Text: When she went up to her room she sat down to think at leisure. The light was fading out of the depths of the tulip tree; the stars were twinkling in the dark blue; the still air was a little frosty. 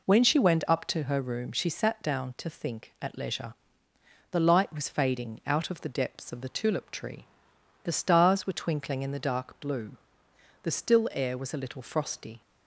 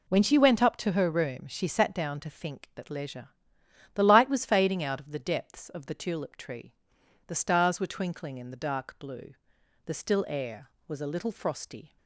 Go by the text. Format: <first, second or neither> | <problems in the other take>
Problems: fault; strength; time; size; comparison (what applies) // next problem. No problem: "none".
neither | none